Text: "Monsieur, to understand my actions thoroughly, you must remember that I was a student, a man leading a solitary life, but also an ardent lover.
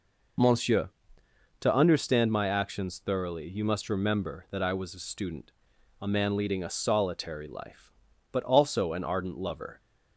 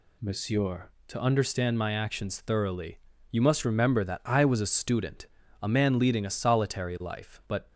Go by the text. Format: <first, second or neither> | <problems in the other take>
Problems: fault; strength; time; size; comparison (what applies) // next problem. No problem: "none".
first | stops before "also an ardent lover"; at 7.7 s